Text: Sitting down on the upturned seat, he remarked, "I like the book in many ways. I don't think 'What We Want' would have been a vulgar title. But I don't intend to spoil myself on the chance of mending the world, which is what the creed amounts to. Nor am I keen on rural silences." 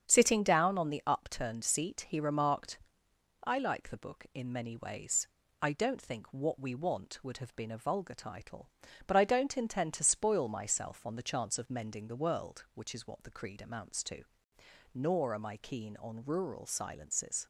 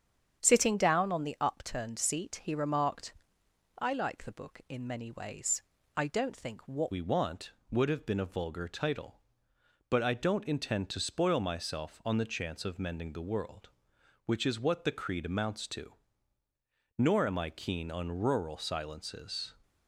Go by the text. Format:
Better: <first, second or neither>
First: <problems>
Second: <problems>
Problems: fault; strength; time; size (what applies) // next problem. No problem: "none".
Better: first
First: starts louder than the rest; strong; until 1.1 s; 8 dB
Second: starts louder than the rest; strong; until 1.4 s; 8 dB // changes voice at "We"; from 6.9 s on; 12.6 s long